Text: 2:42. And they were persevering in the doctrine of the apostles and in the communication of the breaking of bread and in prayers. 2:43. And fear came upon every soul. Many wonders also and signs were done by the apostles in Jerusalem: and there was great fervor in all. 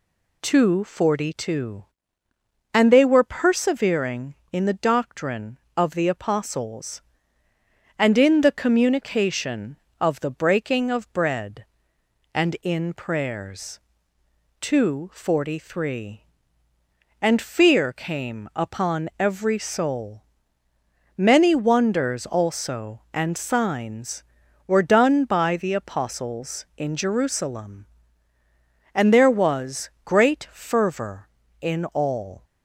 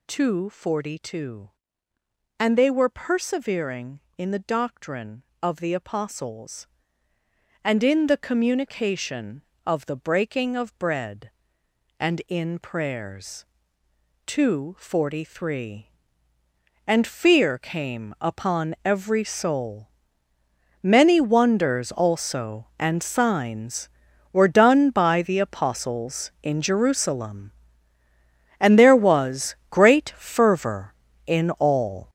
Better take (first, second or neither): first